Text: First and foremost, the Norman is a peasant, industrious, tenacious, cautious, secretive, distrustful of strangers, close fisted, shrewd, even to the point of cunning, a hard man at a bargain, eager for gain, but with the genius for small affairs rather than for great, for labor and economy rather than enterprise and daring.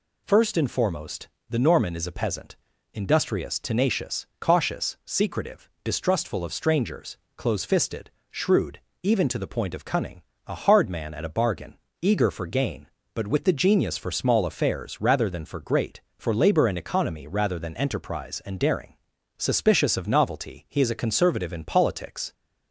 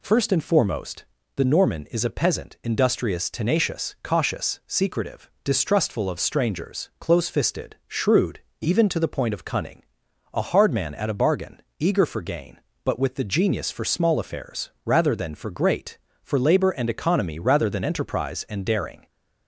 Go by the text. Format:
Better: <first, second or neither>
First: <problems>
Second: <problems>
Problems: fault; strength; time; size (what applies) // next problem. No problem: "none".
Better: second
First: goes on to say "Suspicious of novelty he is a conservative in politics"; strong; from 19.3 s on; 2.9 s long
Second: none